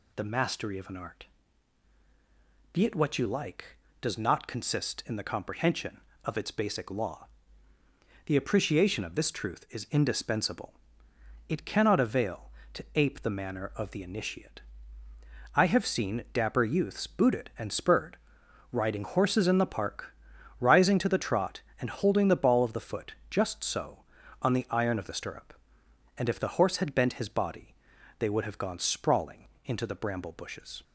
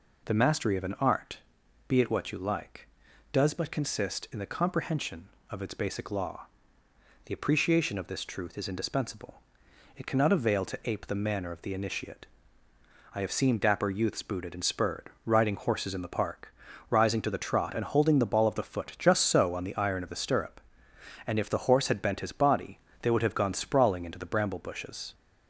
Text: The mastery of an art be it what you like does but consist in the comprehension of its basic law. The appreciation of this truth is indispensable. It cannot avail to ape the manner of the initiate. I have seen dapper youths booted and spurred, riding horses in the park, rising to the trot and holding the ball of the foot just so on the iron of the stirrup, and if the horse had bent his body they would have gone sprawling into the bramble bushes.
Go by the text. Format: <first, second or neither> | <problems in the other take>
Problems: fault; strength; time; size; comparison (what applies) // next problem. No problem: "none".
second | pauses between "art" and "be"; strong; at 1.2 s; 1.4 s long; noticeable in the second // says "not" for "but"; at 4.1 s // pauses between "foot" and "just"; slight; at 23.1 s; 0.16 s long // pauses between "body" and "they"; at 27.7 s; 0.44 s long; slight in the second // pauses between "sprawling" and "into"; slight; at 29.4 s; 0.18 s long